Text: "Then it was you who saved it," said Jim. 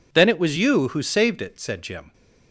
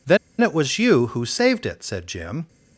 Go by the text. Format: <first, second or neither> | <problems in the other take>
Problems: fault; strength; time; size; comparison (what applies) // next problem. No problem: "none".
first | pauses between "Then" and "it"; slight; at 0.1 s; 0.24 s long